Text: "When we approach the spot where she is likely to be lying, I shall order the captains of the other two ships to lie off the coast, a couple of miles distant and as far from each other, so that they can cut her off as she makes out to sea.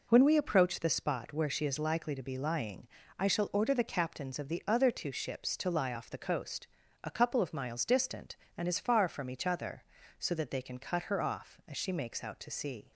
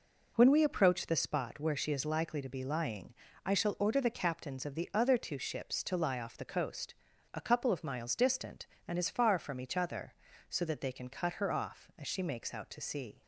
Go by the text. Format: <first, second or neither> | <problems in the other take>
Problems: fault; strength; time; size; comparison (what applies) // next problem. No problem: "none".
neither | none